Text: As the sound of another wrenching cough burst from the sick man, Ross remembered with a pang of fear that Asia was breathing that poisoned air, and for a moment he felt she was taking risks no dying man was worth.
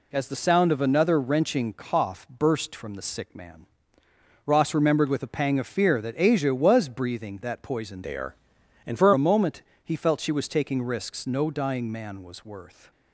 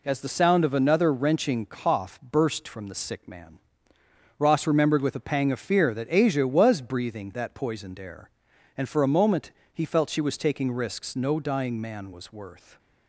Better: second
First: changes voice from "air" to "for"; from 8.0 to 9.1 s; 1.1 s long // pauses between "moment" and "he"; slight; at 9.6 s; 0.20 s long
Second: pauses between "moment" and "he"; slight; at 9.5 s; 0.20 s long

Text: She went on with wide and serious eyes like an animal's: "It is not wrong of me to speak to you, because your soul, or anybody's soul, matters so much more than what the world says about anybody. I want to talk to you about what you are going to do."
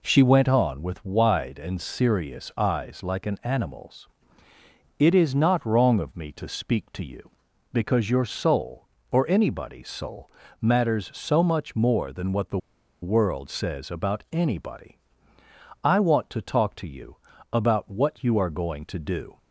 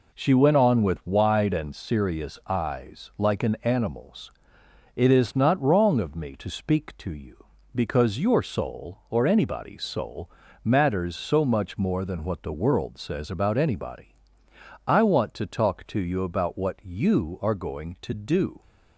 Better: second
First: pauses between "the" and "world"; at 12.5 s; 0.44 s long // pauses between "you" and "about"; slight; at 17.1 s; 0.36 s long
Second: none

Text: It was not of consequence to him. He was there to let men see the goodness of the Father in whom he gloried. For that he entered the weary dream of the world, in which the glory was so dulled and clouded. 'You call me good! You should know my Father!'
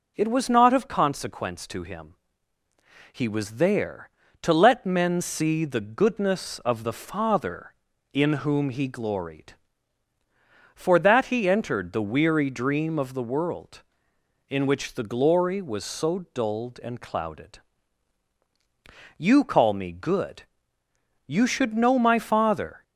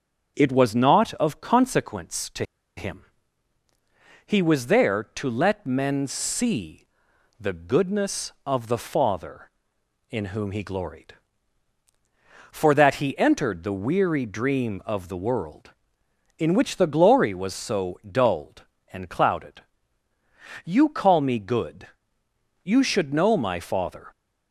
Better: first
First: none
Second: starts louder than the rest; until 1.3 s; 7 dB // pauses between "to" and "him"; slight; at 2.4 s; 0.33 s long // pauses between "see" and "the"; noticeable; at 6.8 s; 0.52 s long

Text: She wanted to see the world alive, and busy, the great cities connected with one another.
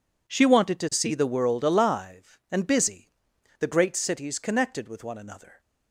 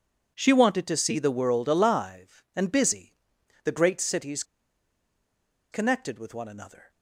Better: first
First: none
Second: pauses between "cities" and "connected"; strong; at 4.4 s; 1.2 s long

